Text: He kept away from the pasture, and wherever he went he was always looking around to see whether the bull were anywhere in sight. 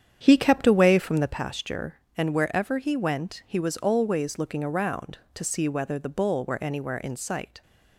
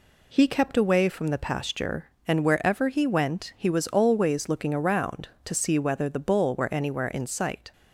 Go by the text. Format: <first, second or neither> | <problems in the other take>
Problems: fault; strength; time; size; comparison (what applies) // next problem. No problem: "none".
second | starts louder than the rest; strong; until 1.4 s; 8.5 dB